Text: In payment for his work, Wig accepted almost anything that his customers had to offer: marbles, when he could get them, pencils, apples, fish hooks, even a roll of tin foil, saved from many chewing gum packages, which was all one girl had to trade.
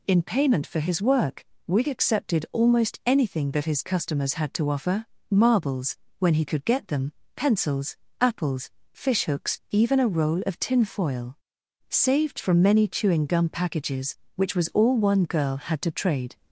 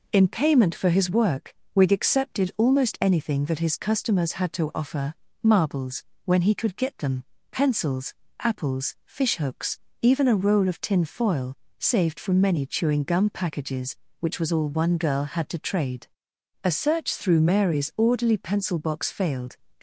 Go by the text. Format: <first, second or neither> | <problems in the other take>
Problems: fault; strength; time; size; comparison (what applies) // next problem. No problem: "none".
first | goes on to say "A search through Mary's orderly pencil box failed"; strong; from 16.6 s on; 2.9 s long